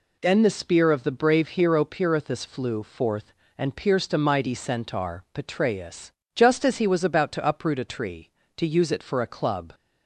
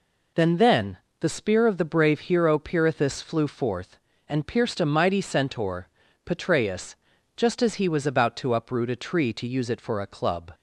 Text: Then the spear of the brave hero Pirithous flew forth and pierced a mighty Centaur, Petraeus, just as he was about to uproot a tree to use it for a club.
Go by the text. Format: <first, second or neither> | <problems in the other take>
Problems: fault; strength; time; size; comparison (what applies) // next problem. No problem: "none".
first | says "Then" twice; at 0.5 s